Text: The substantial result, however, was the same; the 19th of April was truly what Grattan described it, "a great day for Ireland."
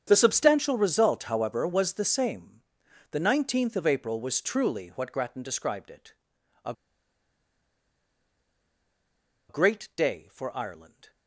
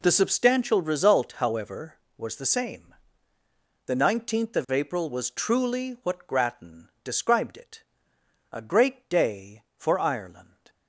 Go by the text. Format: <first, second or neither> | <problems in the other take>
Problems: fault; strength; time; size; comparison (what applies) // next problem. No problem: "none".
second | starts louder than the rest; strong; until 1.0 s; 8 dB // pauses between "a" and "great"; strong; at 6.7 s; 2.7 s long